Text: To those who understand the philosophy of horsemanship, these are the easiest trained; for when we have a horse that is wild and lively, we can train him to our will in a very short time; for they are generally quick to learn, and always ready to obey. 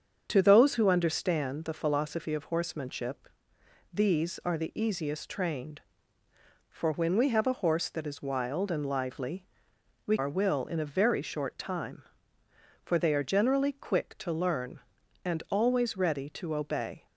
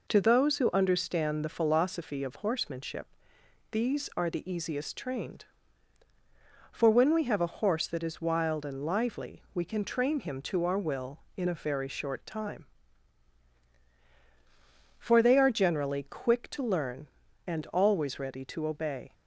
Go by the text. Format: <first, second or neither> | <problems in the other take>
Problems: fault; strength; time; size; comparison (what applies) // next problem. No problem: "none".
second | starts louder than the rest; until 1.2 s; 7 dB // skips "can train him to"; at 10.1 s